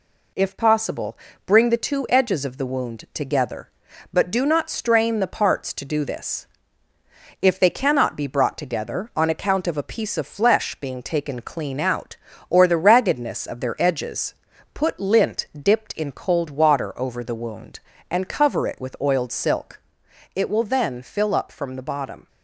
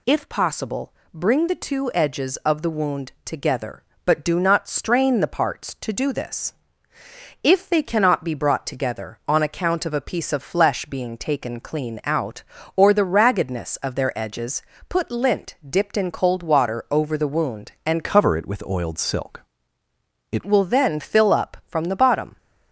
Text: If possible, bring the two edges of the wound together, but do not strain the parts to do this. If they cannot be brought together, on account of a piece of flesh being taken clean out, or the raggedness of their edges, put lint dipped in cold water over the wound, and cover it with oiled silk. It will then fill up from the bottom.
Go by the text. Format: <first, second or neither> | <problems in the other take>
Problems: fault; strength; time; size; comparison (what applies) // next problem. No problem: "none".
first | changes voice from "cover" to "It"; from 18.0 to 20.4 s; 2.4 s long